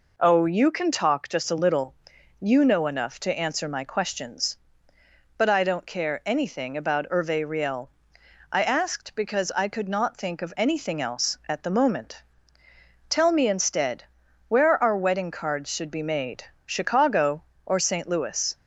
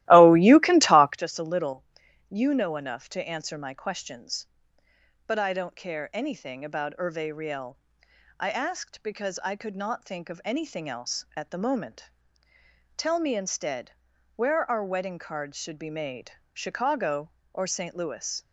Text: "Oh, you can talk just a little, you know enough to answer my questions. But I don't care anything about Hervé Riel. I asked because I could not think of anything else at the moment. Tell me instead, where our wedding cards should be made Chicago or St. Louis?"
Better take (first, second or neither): first